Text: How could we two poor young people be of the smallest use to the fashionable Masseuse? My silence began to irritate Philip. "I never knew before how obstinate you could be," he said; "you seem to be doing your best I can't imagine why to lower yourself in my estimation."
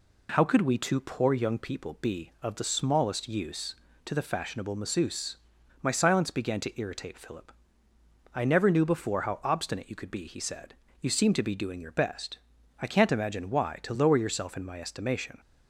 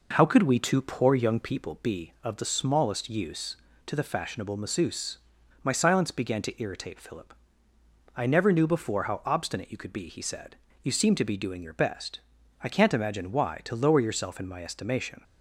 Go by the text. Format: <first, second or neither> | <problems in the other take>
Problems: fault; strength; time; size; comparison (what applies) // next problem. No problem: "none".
first | starts louder than the rest; noticeable; until 1.8 s; 5 dB // pauses between "best" and "I"; at 12.1 s; 0.42 s long; also in the first